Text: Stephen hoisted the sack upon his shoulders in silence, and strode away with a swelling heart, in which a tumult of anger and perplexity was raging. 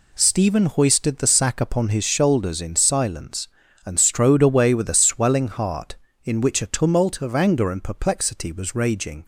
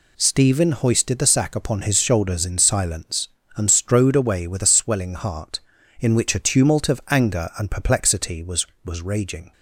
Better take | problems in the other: first | says "was" twice; at 8.8 s

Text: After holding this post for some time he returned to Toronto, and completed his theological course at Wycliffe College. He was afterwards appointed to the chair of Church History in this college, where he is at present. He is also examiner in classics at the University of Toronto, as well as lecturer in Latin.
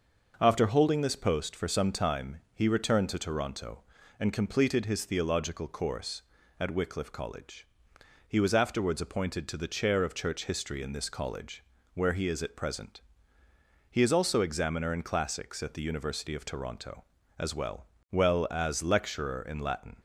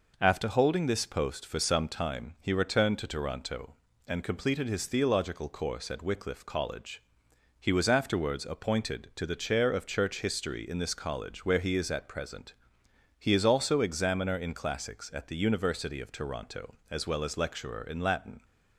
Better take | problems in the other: second | starts louder than the rest; until 1.4 s; 6 dB // says "well" twice; at 18.1 s

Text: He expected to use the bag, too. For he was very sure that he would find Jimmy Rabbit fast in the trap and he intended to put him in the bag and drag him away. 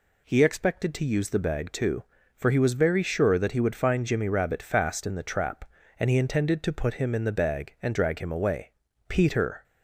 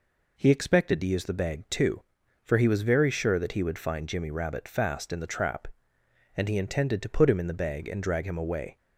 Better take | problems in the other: second | goes on to say "Peter"; from 9.0 s on; 0.56 s long

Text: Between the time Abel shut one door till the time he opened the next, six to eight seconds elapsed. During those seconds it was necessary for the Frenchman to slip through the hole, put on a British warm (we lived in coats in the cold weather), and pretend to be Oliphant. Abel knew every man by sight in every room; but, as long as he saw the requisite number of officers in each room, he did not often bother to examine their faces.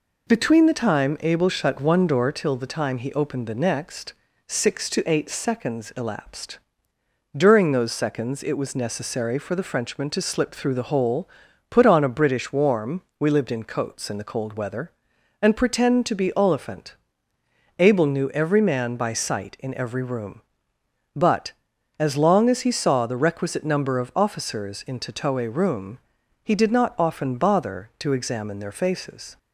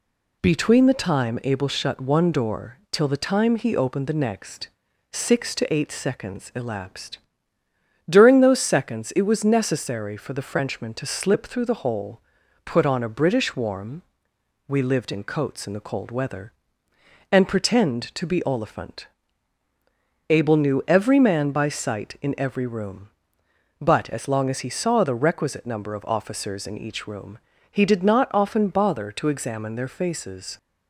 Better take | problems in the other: second | says "tatoe" for "each"; at 24.9 s

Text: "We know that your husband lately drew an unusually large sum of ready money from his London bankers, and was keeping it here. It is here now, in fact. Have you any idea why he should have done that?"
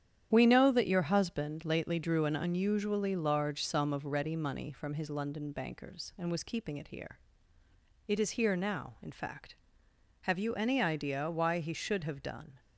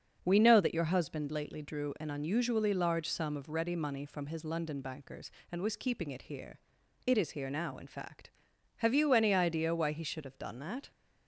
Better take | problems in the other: second | starts louder than the rest; strong; until 1.3 s; 9.5 dB; also in the second // stops before "that"; at 12.5 s

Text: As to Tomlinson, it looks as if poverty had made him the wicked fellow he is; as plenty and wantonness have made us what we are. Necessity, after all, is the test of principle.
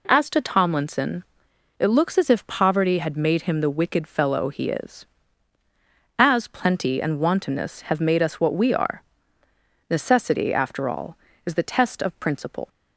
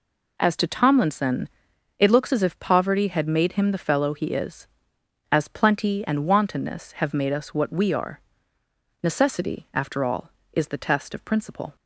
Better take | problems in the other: first | skips "wicked"; at 3.7 s

